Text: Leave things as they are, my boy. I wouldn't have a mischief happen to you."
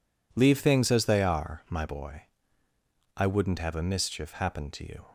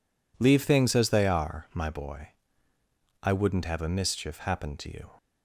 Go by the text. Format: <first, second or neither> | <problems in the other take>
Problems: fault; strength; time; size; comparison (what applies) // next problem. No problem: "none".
neither | none